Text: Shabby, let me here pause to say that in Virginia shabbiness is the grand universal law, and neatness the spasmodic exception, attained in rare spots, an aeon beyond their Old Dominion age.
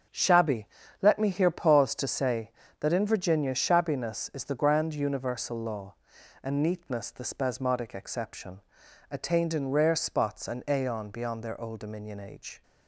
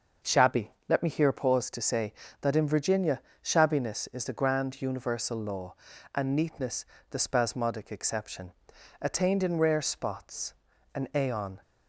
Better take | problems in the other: first | starts louder than the rest; noticeable; until 1.4 s; 6 dB; strong in the first // pauses between "Virginia" and "shabbiness"; slight; at 3.2 s; 0.22 s long // pauses between "neatness" and "the"; slight; at 6.8 s; 0.24 s long // stops before "beyond their Old Dominion age"; at 11.6 s

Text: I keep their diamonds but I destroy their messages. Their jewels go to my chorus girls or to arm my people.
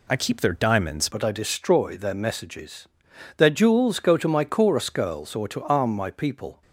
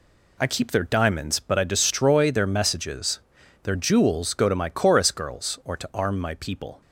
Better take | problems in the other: second | changes voice at "but"; from 1.1 s on; 5.5 s long

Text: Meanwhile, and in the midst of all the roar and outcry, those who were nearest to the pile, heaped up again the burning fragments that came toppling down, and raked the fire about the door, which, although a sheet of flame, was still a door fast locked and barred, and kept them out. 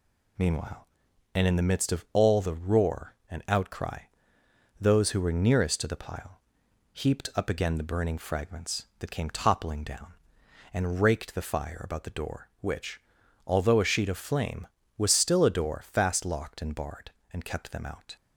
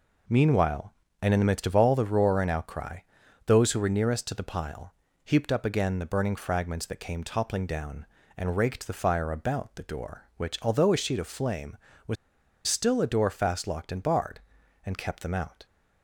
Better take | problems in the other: first | pauses between "was" and "still"; noticeable; at 12.1 s; 0.51 s long

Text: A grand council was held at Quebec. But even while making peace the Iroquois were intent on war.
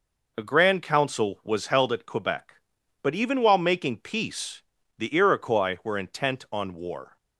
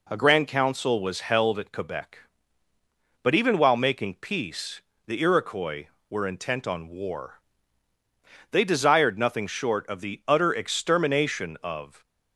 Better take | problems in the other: first | pauses between "peace" and "the"; slight; at 4.7 s; 0.26 s long; slight in the first // goes on to say "They desired nothing short of the utter extermination of"; strong; from 8.5 s on; 3.5 s long

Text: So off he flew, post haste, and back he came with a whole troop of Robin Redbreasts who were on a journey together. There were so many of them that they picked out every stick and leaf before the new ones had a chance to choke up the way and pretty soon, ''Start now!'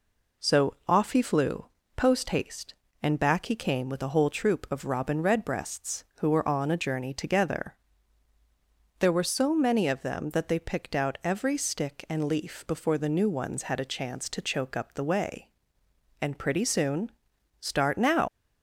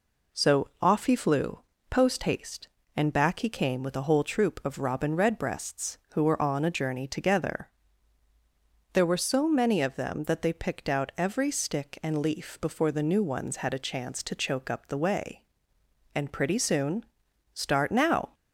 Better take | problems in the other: second | leaves "now" unfinished; at 18.2 s; 115 ms

